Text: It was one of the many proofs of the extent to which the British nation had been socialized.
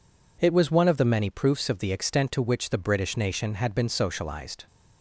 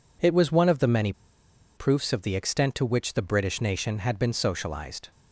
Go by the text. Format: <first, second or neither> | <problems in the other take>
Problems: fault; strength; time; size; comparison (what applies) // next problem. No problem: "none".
first | pauses between "many" and "proofs"; noticeable; at 1.1 s; 0.62 s long